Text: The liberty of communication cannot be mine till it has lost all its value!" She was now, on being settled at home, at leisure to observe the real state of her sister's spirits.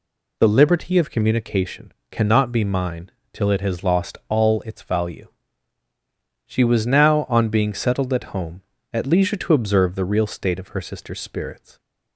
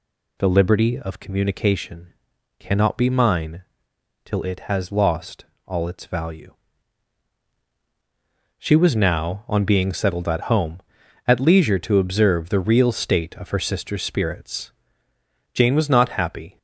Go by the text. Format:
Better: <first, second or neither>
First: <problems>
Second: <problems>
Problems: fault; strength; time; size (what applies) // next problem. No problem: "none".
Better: first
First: pauses between "communication" and "cannot"; slight; at 1.9 s; 0.20 s long // pauses between "mine" and "till"; slight; at 3.0 s; 0.24 s long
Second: pauses between "communication" and "cannot"; noticeable; at 2.1 s; 0.46 s long // pauses between "mine" and "till"; noticeable; at 3.6 s; 0.60 s long // pauses between "lost" and "all"; slight; at 5.4 s; 0.20 s long // goes on to say "Jane was not happy"; noticeable; from 15.5 s on; 1.0 s long